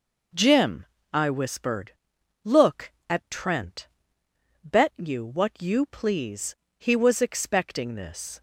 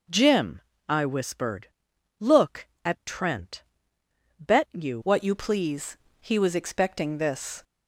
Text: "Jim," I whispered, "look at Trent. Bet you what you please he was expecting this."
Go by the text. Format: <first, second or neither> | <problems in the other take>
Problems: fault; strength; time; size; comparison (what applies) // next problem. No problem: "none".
first | changes voice at "what"; from 5.0 s on; 2.6 s long // pauses between "please" and "he"; slight; at 5.9 s; 0.24 s long; slight in the first